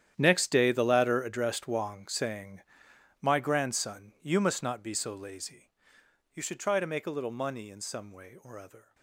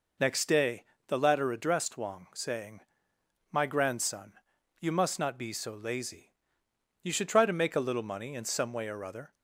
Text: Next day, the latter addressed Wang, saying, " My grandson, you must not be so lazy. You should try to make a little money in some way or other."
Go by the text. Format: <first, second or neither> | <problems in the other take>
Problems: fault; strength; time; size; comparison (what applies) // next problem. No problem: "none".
second | gets quieter; strong; throughout; 15 dB